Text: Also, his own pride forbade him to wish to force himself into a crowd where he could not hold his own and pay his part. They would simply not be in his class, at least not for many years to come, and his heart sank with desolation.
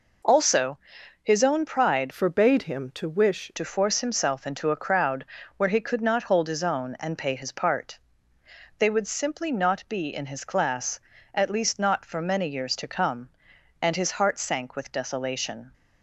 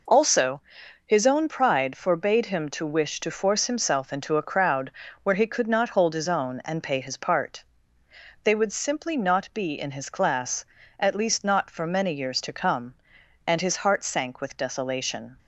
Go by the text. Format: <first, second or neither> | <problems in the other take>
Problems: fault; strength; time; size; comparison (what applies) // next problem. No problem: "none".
second | changes voice from "forbade" to "wish"; from 2.1 to 3.5 s; 1.4 s long // pauses between "crowd" and "where"; slight; at 5.2 s; 0.32 s long; slight in the second